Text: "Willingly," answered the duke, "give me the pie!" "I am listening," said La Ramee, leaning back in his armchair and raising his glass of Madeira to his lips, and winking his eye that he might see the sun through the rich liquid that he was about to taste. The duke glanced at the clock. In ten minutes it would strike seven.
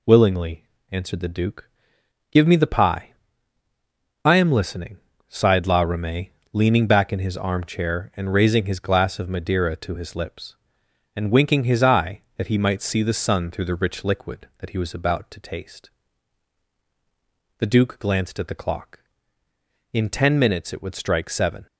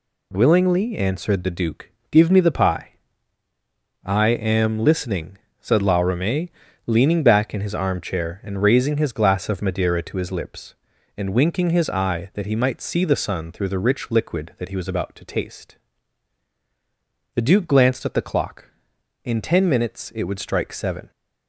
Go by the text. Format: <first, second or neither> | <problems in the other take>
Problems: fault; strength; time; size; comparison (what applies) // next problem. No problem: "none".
second | says "sighed" for "said"; at 5.2 s